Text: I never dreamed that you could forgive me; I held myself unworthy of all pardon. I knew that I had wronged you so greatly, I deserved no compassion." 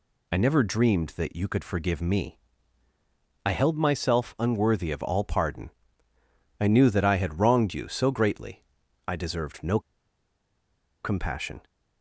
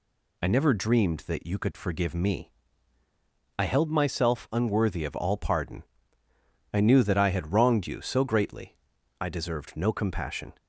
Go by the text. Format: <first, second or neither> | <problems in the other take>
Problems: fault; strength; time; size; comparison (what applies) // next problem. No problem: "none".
second | pauses between "no" and "compassion"; at 9.7 s; 1.2 s long